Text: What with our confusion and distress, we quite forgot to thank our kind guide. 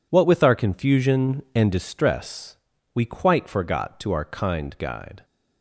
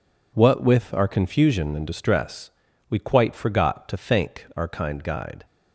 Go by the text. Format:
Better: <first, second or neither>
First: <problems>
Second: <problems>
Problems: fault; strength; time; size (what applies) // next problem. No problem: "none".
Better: second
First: skips "thank"; at 4.1 s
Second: none